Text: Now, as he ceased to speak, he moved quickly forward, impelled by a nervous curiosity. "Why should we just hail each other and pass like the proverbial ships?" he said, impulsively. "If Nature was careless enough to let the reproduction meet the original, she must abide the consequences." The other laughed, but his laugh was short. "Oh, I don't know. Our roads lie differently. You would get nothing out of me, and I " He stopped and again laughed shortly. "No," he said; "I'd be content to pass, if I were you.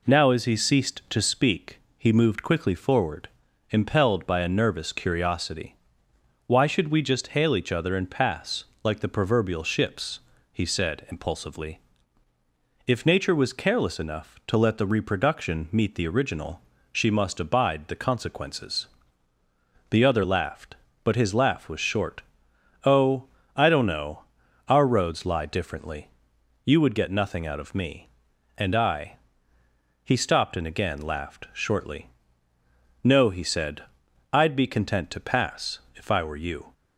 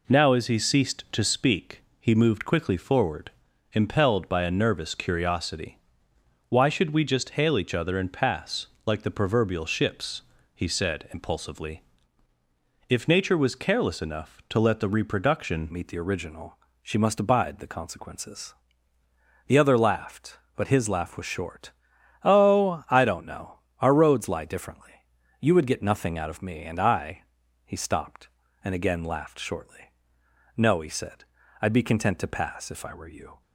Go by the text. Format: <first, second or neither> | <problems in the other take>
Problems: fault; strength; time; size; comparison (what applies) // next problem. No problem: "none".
first | pauses between "pass" and "like"; slight; at 8.6 s; 0.18 s long; slight in the first // changes voice at "meet"; from 15.7 s on; 17.7 s long